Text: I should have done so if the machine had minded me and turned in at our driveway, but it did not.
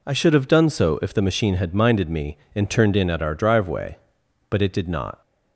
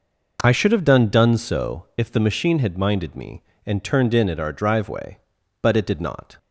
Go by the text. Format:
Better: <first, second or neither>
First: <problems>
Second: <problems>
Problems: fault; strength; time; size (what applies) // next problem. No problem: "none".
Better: first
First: none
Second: says "done" twice; at 1.0 s